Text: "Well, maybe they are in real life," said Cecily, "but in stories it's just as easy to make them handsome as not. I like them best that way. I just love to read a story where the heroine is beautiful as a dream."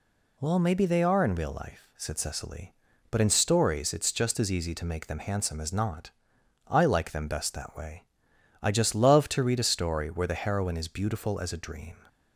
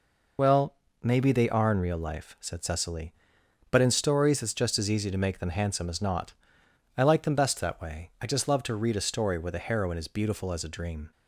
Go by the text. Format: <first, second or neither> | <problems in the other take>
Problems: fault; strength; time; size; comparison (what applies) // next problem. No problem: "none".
first | loses the start of "Well"; at 0.3 s; 40 ms